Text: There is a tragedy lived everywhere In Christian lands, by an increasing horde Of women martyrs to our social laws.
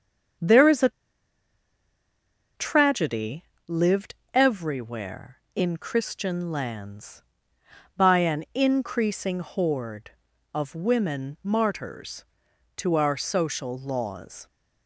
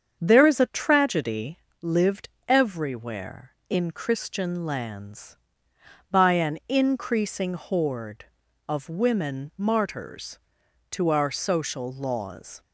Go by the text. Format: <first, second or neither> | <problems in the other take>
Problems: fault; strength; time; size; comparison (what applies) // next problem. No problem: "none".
second | starts louder than the rest; strong; until 3.0 s; 7.5 dB; strong in the second // pauses between "a" and "tragedy"; strong; at 0.8 s; 1.6 s long // pauses between "tragedy" and "lived"; slight; at 3.4 s; 0.22 s long; slight in the second // pauses between "lived" and "everywhere"; slight; at 4.1 s; 0.18 s long; slight in the second